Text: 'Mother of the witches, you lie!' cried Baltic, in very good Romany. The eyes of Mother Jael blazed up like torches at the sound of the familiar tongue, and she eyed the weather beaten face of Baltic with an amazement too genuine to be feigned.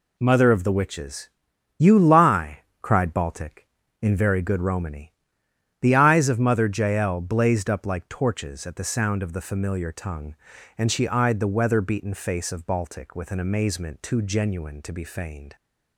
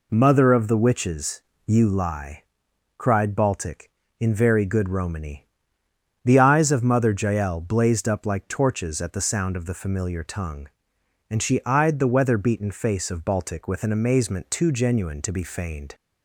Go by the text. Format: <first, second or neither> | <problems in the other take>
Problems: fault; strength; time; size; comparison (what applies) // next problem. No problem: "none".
neither | none